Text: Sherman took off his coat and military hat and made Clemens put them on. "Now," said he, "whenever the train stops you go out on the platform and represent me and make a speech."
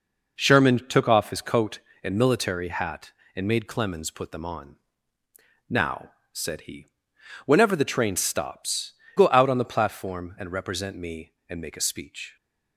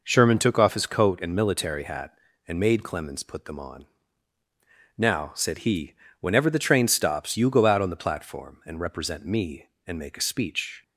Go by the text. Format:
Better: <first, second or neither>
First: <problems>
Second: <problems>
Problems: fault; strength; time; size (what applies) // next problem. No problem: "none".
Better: second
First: skips "you"; at 9.0 s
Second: none